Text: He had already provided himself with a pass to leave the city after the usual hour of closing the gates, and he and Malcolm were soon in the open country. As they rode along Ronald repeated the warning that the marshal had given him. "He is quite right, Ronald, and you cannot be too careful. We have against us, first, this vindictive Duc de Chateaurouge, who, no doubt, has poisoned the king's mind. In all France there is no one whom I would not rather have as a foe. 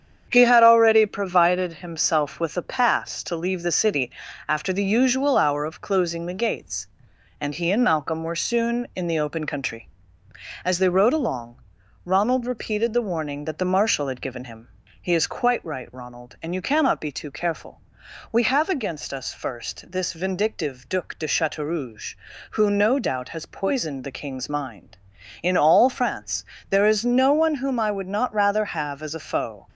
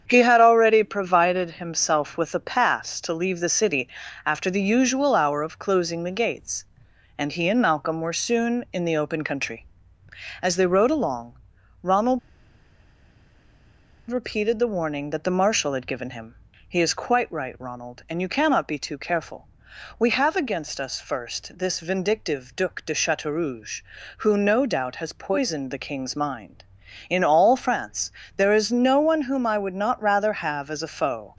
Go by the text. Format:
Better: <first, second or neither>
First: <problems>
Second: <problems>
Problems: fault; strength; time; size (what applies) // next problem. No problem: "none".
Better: first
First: starts louder than the rest; strong; until 1.3 s; 8 dB // pauses between "city" and "after"; slight; at 4.1 s; 0.36 s long // pauses between "along" and "Ronald"; at 11.6 s; 0.42 s long // pauses between "France" and "there"; slight; at 26.4 s; 0.26 s long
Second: starts louder than the rest; strong; until 1.0 s; 8 dB // pauses between "city" and "after"; slight; at 3.8 s; 0.36 s long // pauses between "along" and "Ronald"; at 11.3 s; 0.42 s long // pauses between "Ronald" and "repeated"; strong; at 12.1 s; 1.9 s long // pauses between "France" and "there"; slight; at 28.0 s; 0.26 s long